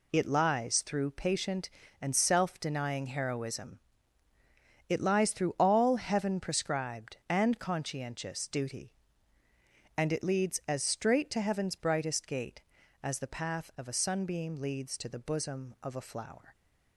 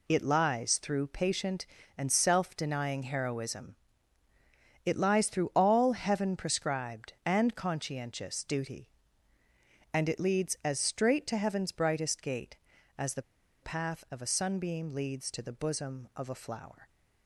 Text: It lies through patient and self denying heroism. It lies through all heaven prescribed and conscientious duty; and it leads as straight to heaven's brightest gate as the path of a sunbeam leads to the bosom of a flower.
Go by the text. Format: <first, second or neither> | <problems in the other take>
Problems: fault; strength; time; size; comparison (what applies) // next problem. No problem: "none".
first | pauses between "the" and "path"; at 13.2 s; 0.40 s long